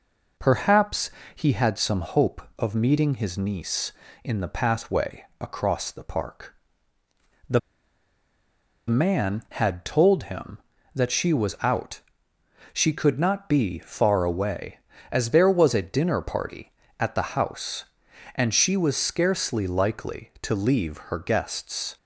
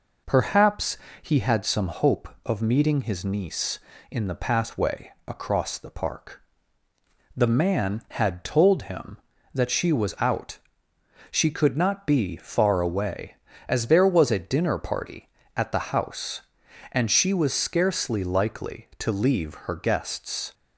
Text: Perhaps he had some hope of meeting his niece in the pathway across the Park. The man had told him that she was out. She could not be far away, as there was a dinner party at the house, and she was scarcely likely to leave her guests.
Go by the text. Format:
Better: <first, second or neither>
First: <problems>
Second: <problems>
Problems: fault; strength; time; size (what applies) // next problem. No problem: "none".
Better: second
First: pauses between "Perhaps" and "he"; slight; at 1.0 s; 0.26 s long // pauses between "pathway" and "across"; slight; at 5.2 s; 0.16 s long // pauses between "The" and "man"; strong; at 7.5 s; 1.2 s long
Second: pauses between "Perhaps" and "he"; slight; at 0.9 s; 0.26 s long // pauses between "pathway" and "across"; slight; at 5.1 s; 0.16 s long